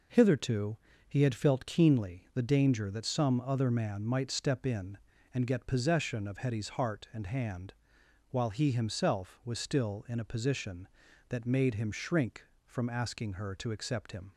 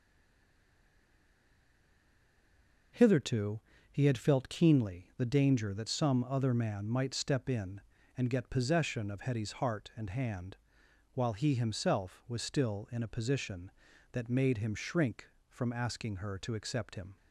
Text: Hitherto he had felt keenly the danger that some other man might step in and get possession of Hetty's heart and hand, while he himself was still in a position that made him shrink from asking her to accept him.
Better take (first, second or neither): first